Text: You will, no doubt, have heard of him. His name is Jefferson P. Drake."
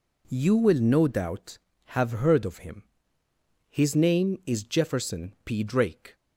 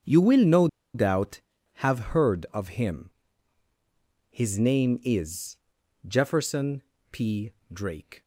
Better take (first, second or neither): first